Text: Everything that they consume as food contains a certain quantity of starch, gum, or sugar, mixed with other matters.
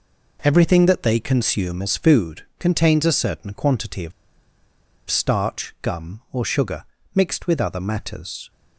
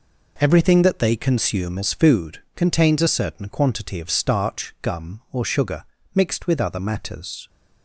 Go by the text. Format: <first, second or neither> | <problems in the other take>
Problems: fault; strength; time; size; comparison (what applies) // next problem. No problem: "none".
second | pauses between "of" and "starch"; noticeable; at 4.1 s; 0.97 s long